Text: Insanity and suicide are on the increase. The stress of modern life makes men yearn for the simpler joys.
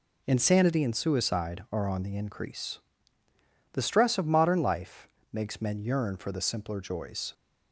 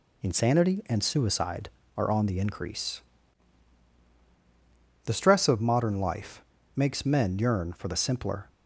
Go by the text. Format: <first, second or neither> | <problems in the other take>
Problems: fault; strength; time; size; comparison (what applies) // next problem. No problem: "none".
first | pauses between "life" and "makes"; slight; at 6.4 s; 0.32 s long; slight in the first // stops before "joys"; at 8.4 s